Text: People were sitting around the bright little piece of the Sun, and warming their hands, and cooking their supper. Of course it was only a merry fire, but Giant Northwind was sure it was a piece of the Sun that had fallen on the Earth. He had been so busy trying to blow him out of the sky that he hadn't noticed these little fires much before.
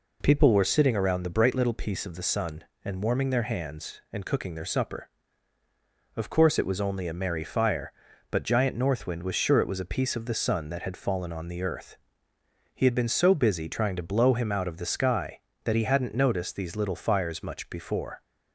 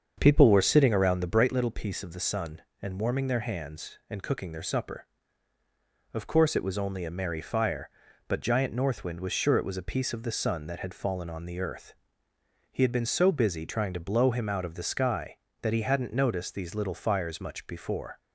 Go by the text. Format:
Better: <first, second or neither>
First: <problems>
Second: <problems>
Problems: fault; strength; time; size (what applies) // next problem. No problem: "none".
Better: first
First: none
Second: starts louder than the rest; until 1.6 s; 7 dB